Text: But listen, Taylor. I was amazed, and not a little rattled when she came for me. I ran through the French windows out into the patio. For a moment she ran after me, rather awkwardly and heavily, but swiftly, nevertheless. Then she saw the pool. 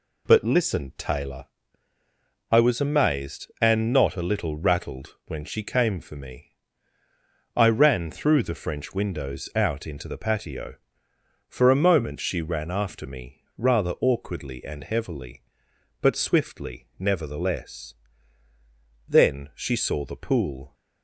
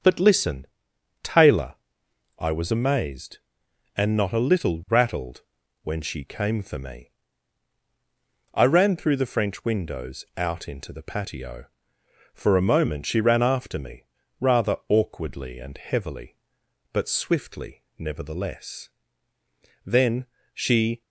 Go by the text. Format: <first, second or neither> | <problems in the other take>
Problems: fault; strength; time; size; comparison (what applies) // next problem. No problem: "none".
first | starts louder than the rest; until 1.6 s; 6.5 dB // pauses between "rattled" and "when"; at 5.4 s; 0.42 s long // pauses between "Then" and "she"; slight; at 20.2 s; 0.28 s long // stops before "saw the pool"; at 21.0 s